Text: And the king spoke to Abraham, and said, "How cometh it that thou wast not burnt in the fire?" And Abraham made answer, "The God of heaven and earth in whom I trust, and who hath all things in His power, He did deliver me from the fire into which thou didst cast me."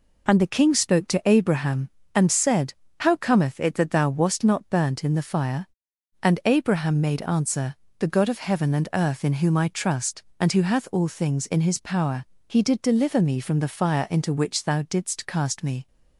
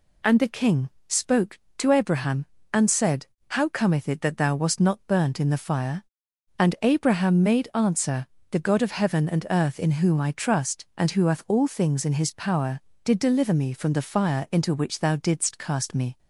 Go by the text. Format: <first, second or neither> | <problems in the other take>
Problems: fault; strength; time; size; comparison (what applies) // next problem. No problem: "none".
first | pauses between "king" and "spoke"; slight; at 0.8 s; 0.18 s long // skips "He"; at 12.9 s